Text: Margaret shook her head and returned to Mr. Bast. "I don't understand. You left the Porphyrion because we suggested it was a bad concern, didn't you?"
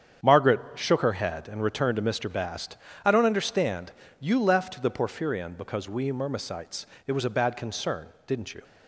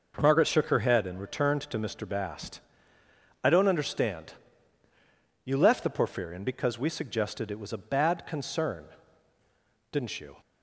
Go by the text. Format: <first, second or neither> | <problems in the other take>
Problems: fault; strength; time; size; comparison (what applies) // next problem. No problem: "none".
second | starts louder than the rest; strong; until 1.3 s; 8.5 dB // pauses between "Margaret" and "shook"; slight; at 0.5 s; 0.16 s long // says "myrmecites" for "suggested"; at 6.1 s